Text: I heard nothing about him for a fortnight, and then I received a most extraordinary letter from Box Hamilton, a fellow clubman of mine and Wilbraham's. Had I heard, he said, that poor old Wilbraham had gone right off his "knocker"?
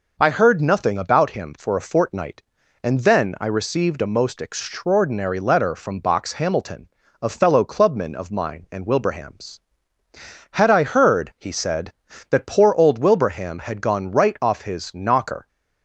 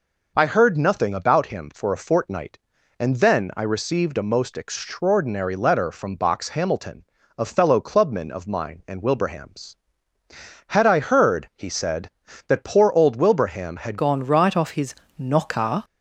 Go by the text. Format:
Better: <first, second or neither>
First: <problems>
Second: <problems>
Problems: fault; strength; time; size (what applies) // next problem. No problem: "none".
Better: first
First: none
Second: changes voice at "gone"; from 13.9 s on; 1.9 s long // pauses between "his" and "knocker"; slight; at 14.9 s; 0.24 s long